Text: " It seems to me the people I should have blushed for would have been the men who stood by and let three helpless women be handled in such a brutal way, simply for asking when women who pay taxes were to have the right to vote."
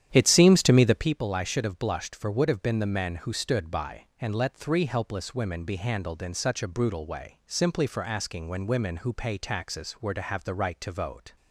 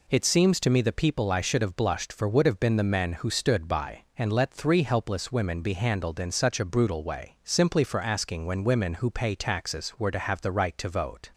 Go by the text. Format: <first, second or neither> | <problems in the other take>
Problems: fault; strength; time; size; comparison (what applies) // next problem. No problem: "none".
second | starts louder than the rest; strong; until 1.1 s; 10 dB